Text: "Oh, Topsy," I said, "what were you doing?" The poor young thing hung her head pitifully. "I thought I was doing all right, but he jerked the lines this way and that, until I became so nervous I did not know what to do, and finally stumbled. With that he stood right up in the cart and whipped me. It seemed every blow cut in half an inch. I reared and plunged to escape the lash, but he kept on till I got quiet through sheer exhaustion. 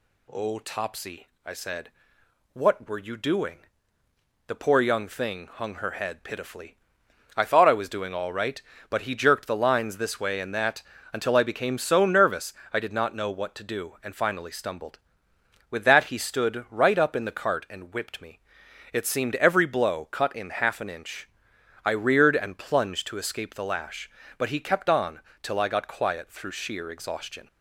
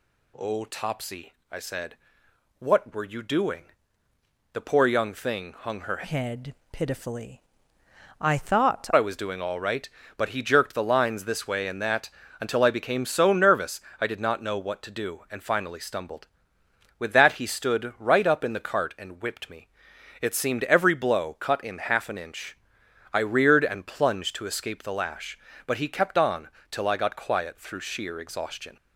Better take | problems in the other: first | changes voice from "head" to "thought"; from 6.0 to 8.8 s; 2.8 s long // pauses between "head" and "pitifully"; slight; at 6.5 s; 0.18 s long // pauses between "nervous" and "I"; slight; at 13.8 s; 0.18 s long; slight in the first // pauses between "on" and "till"; slight; at 26.5 s; 0.20 s long; slight in the first

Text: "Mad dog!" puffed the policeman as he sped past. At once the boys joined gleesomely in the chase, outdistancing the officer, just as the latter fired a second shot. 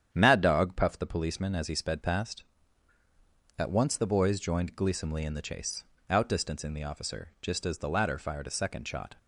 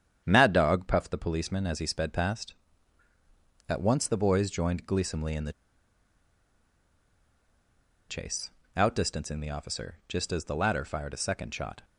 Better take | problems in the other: first | starts louder than the rest; strong; until 1.2 s; 9 dB; strong in the first // pauses between "the" and "chase"; strong; at 5.5 s; 2.5 s long

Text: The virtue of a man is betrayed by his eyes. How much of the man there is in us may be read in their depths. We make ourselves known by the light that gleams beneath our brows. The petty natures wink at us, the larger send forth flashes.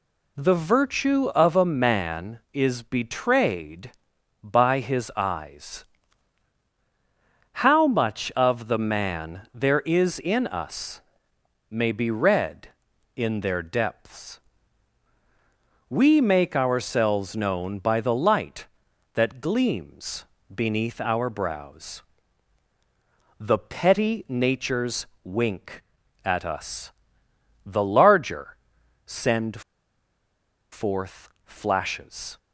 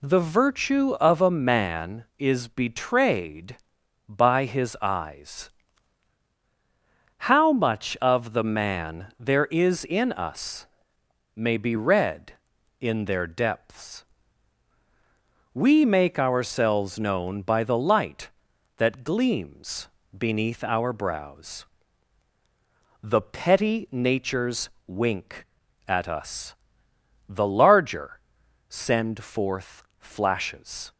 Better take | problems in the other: second | pauses between "us" and "may"; noticeable; at 11.0 s; 0.68 s long; noticeable in the second // pauses between "gleams" and "beneath"; slight; at 20.2 s; 0.28 s long; slight in the second // pauses between "natures" and "wink"; slight; at 25.0 s; 0.18 s long; slight in the second // pauses between "larger" and "send"; noticeable; at 28.5 s; 0.48 s long; noticeable in the second // pauses between "send" and "forth"; at 29.6 s; 1.1 s long // pauses between "forth" and "flashes"; slight; at 31.2 s; 0.16 s long; slight in the second

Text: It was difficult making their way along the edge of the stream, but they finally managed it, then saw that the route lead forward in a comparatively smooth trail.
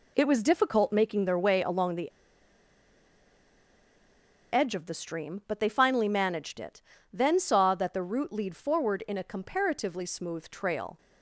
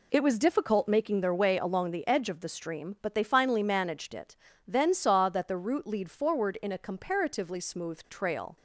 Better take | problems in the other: second | pauses between "the" and "edge"; strong; at 2.1 s; 2.4 s long

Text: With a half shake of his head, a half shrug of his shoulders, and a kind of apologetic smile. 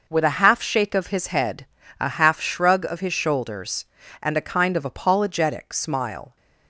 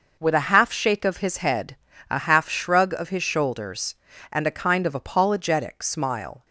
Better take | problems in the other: neither | none

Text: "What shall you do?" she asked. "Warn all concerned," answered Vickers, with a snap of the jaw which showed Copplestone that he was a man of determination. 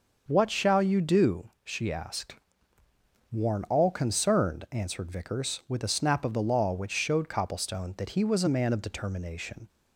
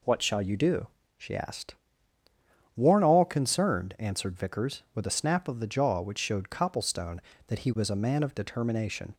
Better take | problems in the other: second | starts louder than the rest; until 1.2 s; 6 dB // says "law" for "jaw"; at 6.4 s

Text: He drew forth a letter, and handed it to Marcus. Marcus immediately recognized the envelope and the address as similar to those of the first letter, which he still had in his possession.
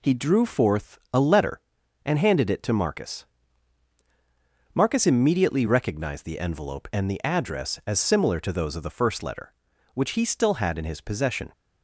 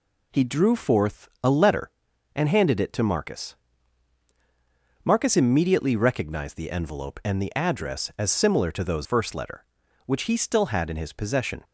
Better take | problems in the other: first | pauses between "forth" and "a"; slight; at 1.2 s; 0.16 s long; slight in the first // skips "of the"; at 9.0 s

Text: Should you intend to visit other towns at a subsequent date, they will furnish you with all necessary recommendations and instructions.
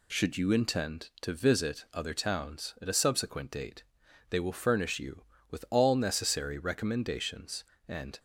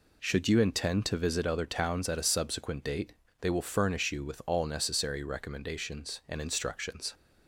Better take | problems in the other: second | stops before "instructions"; at 8.1 s

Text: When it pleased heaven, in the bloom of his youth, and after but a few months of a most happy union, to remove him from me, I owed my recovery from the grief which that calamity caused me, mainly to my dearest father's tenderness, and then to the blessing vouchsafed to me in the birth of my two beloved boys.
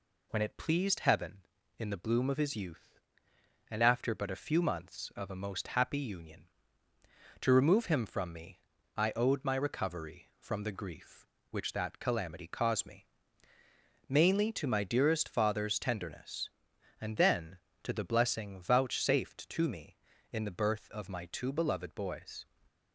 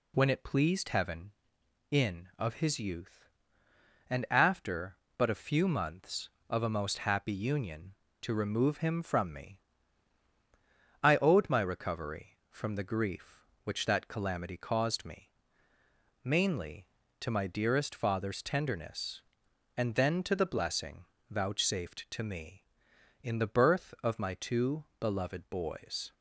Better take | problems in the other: first | skips "the bloom"; at 2.3 s // pauses between "blessing" and "vouchsafed"; slight; at 21.0 s; 0.26 s long // pauses between "two" and "beloved"; slight; at 24.8 s; 0.16 s long

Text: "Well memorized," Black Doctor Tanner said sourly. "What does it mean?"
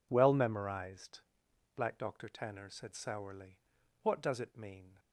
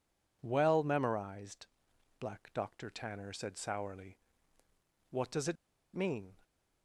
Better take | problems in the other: first | pauses between "it" and "mean"; at 5.5 s; 0.40 s long

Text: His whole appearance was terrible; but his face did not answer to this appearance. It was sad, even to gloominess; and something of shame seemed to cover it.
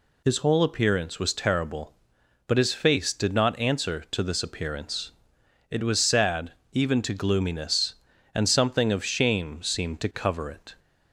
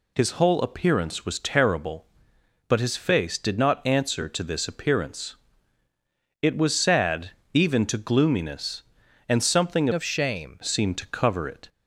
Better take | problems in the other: first | changes voice from "of" to "shame"; from 9.9 to 10.5 s; 0.6 s long

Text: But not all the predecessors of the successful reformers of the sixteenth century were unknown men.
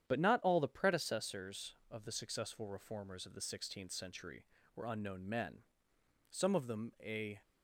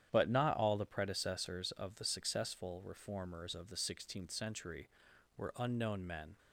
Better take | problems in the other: second | starts louder than the rest; strong; until 1.1 s; 9.5 dB; strong in the second // goes on to say "Some of them a"; noticeable; from 6.3 s on; 1.0 s long

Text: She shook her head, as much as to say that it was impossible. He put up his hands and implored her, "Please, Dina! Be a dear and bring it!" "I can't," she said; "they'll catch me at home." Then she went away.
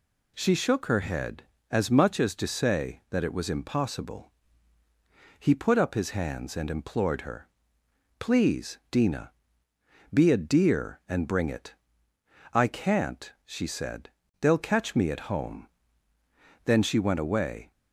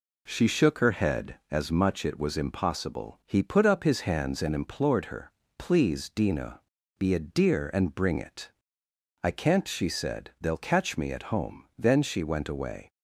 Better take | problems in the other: first | skips "as to say that"; at 2.0 s

